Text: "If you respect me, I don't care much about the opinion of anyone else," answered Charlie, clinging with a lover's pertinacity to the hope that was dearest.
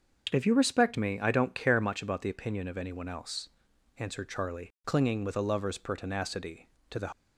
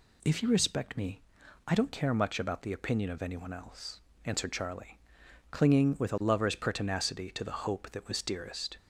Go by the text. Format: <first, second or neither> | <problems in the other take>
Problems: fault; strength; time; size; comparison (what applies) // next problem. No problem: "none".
second | starts louder than the rest; until 1.3 s; 6.5 dB // stops before "hope that was dearest"; at 7.1 s